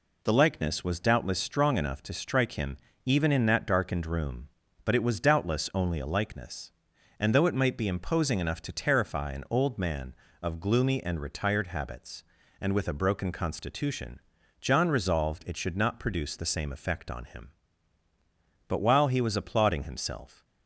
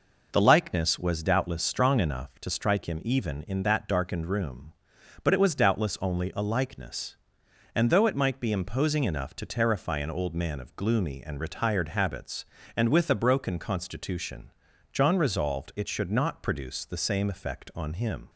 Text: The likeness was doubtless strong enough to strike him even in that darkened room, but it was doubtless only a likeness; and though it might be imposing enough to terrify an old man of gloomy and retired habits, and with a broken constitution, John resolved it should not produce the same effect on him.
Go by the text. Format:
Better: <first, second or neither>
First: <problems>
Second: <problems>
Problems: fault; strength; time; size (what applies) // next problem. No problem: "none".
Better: second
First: pauses between "him" and "even"; slight; at 2.7 s; 0.28 s long // goes on to say "But while he was applauding himself"; strong; from 18.6 s on; 1.7 s long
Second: none